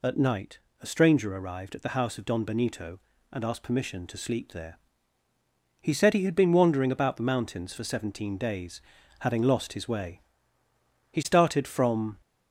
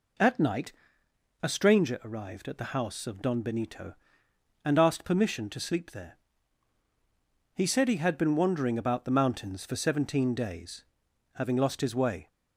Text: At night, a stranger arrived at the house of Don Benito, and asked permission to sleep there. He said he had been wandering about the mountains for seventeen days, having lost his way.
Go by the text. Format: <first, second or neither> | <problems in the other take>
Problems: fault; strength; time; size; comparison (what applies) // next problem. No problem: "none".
second | goes on to say "He started from"; noticeable; from 11.1 s on; 1.0 s long